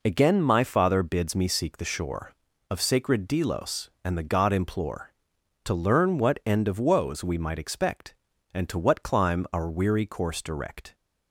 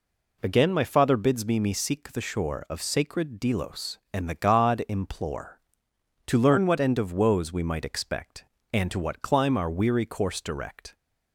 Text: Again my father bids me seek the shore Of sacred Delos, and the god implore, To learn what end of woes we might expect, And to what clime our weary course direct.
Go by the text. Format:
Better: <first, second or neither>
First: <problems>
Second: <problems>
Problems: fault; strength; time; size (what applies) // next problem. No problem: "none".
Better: first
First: none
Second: says "me" twice; at 1.5 s